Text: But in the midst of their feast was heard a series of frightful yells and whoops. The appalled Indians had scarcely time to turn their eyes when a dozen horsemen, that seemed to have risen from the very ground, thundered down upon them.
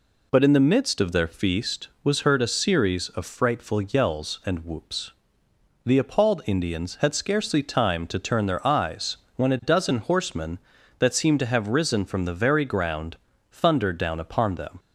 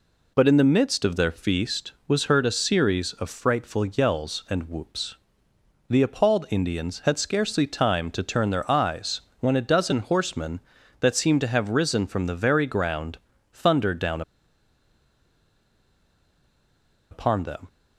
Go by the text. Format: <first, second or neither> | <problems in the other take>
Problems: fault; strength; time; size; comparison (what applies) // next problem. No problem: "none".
first | pauses between "eyes" and "when"; slight; at 9.2 s; 0.20 s long; slight in the first // pauses between "down" and "upon"; strong; at 14.2 s; 2.8 s long